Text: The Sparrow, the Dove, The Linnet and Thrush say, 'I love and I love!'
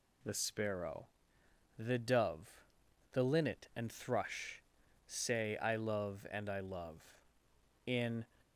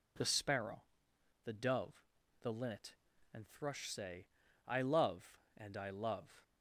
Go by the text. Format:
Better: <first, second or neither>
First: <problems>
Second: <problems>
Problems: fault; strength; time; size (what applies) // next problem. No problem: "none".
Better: second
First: pauses between "Thrush" and "say"; noticeable; at 4.6 s; 0.46 s long // goes on to say "In"; slight; from 7.8 s on; 0.38 s long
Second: none